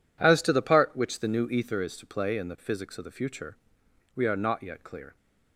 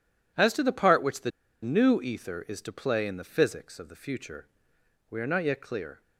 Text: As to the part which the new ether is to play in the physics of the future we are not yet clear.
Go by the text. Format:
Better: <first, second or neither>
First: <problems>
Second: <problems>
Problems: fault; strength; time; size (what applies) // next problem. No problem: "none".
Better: first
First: pauses between "future" and "we"; noticeable; at 3.5 s; 0.56 s long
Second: pauses between "the" and "new"; slight; at 1.3 s; 0.32 s long // pauses between "future" and "we"; noticeable; at 4.4 s; 0.64 s long